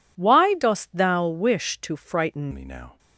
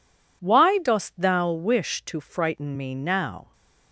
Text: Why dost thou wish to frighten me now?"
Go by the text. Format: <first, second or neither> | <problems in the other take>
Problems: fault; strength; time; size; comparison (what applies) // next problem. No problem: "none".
second | changes voice at "me"; from 2.5 s on; 0.4 s long